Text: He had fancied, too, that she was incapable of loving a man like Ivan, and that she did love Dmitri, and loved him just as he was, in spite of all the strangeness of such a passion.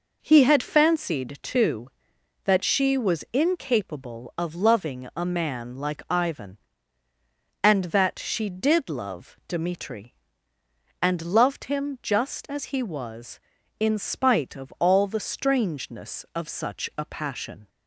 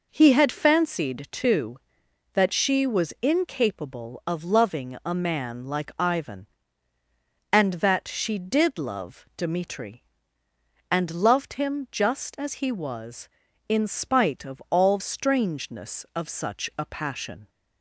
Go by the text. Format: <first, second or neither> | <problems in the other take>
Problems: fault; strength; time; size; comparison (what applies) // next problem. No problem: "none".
first | skips "the"; at 14.9 s